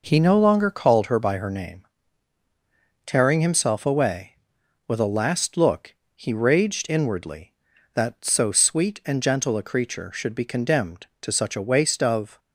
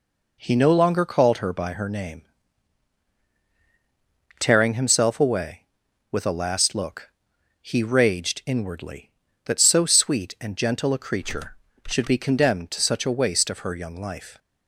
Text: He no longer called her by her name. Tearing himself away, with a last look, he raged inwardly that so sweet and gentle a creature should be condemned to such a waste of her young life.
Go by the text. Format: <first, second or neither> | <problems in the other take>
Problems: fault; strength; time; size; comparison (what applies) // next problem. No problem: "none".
second | stops before "her young life"; at 12.3 s